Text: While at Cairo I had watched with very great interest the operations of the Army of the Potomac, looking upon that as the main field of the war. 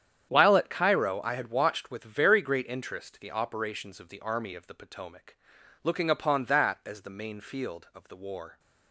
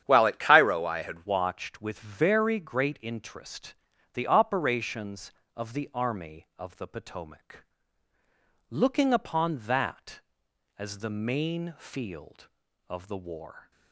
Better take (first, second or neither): first